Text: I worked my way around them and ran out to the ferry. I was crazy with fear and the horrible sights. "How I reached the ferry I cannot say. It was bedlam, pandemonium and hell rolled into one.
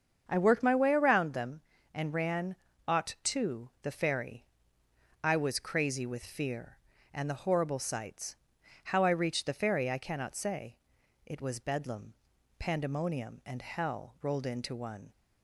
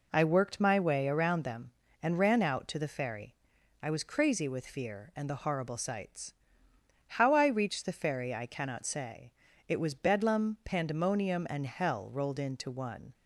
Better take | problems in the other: second | starts louder than the rest; strong; until 1.2 s; 7 dB // says "ought" for "out"; at 2.8 s

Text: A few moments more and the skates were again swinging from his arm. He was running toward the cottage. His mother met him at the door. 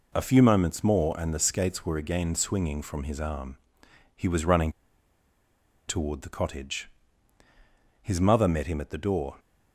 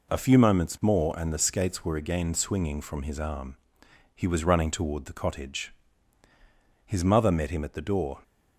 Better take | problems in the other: second | pauses between "running" and "toward"; at 4.6 s; 1.1 s long

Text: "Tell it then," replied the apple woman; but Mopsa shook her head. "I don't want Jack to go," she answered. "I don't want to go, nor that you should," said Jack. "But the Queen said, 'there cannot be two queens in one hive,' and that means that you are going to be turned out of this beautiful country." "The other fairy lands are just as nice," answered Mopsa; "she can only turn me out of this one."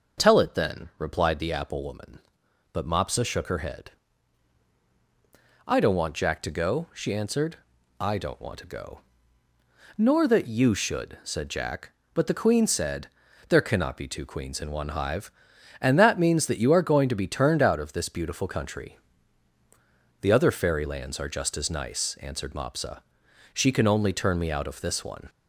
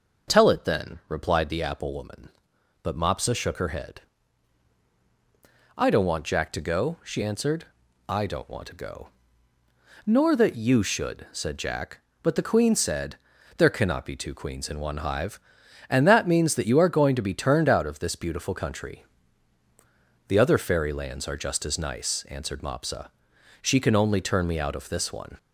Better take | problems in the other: neither | none

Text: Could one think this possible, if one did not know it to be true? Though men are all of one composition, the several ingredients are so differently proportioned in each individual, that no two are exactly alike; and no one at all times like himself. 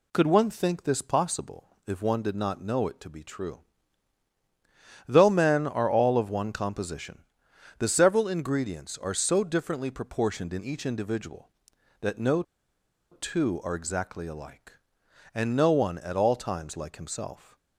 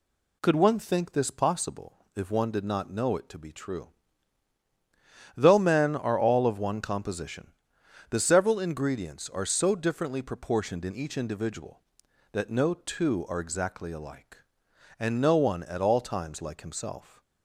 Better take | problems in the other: second | pauses between "no" and "two"; noticeable; at 12.4 s; 0.69 s long

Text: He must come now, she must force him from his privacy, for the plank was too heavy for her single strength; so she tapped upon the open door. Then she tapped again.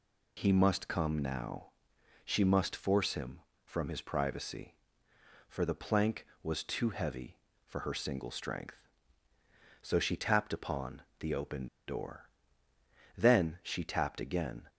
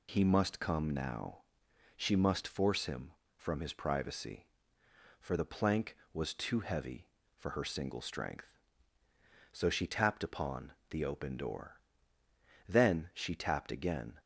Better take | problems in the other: second | pauses between "upon" and "the"; slight; at 11.0 s; 0.16 s long; slight in the second // pauses between "open" and "door"; slight; at 11.6 s; 0.21 s long

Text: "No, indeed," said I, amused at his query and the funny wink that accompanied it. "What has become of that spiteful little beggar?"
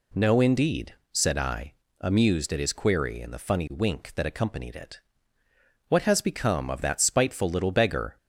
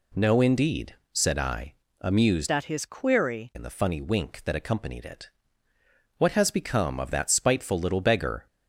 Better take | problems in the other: first | changes voice from "at" to "query"; from 2.5 to 3.5 s; 1.0 s long

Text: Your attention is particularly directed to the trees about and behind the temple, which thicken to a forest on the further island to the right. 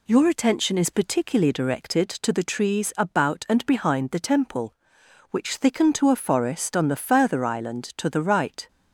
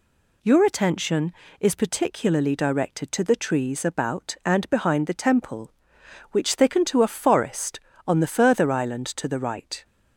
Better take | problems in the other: neither | none

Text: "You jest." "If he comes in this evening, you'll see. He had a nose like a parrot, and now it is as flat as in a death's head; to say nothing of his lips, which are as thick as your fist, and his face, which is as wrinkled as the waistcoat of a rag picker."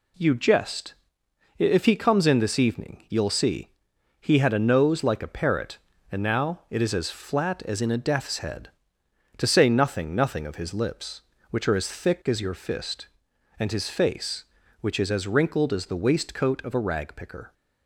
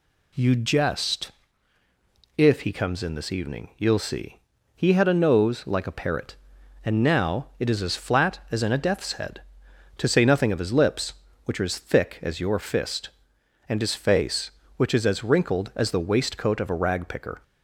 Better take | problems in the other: second | says "nothing" twice; at 10.1 s

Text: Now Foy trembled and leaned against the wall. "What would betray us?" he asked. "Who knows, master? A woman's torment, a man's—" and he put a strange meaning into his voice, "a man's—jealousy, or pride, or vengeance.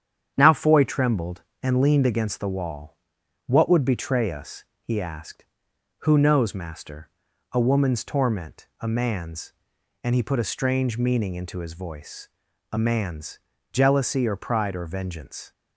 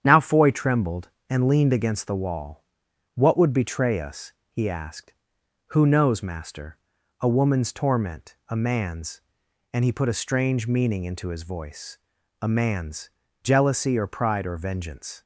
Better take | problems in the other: neither | starts louder than the rest; strong; the same in both

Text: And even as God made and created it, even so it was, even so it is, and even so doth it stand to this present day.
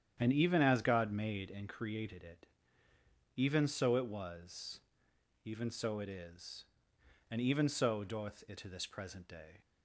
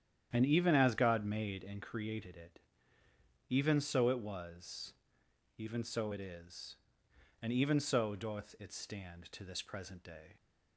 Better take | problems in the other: second | starts louder than the rest; strong; until 1.1 s; 9.5 dB; strong in the second // skips "stand"; at 8.5 s

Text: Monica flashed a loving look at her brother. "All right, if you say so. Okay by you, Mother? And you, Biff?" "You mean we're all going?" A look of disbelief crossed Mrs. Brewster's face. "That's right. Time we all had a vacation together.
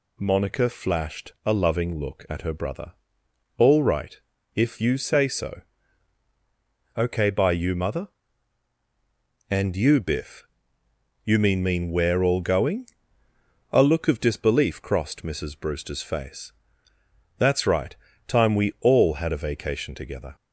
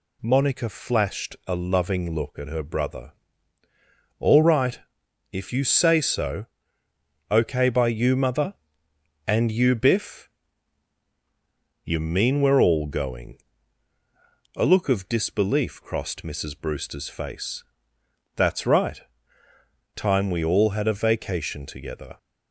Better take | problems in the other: second | says "mean" twice; at 11.6 s

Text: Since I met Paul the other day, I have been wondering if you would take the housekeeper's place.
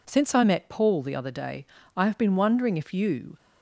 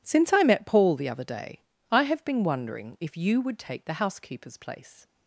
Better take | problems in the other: second | stops before "would take the housekeeper's place"; at 3.3 s

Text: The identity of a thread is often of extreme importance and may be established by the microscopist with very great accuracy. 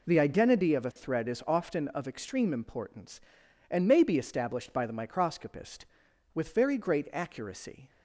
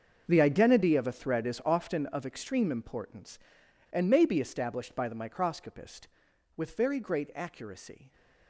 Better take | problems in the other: first | gets quieter; strong; throughout; 14.5 dB

